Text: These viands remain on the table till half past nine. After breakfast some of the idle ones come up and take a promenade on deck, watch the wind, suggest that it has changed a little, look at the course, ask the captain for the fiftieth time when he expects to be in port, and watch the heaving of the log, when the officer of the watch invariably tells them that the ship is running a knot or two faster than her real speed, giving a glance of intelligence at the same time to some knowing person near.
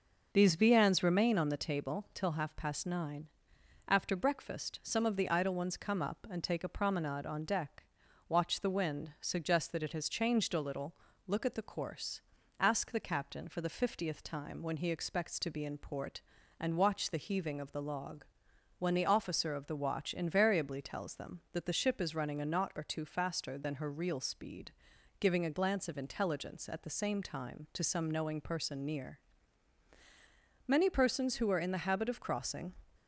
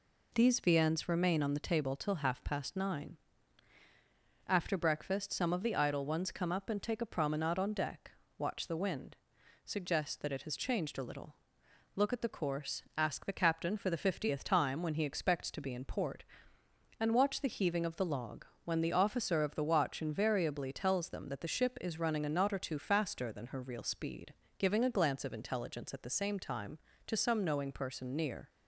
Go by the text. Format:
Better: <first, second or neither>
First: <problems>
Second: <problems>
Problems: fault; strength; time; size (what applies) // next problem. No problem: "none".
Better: second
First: goes on to say "Many persons who are in the habit of crossing"; strong; from 30.6 s on; 2.0 s long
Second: none